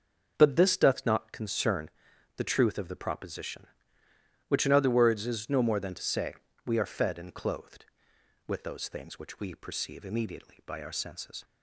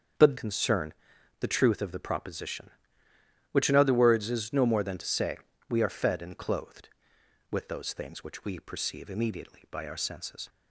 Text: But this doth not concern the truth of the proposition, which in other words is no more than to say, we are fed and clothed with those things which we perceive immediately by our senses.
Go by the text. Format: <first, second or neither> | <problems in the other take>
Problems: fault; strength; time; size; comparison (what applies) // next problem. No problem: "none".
first | starts louder than the rest; strong; until 1.6 s; 7 dB; also in the first // skips "this doth not"; at 0.3 s // pauses between "concern" and "the"; noticeable; at 0.9 s; 0.48 s long; noticeable in the first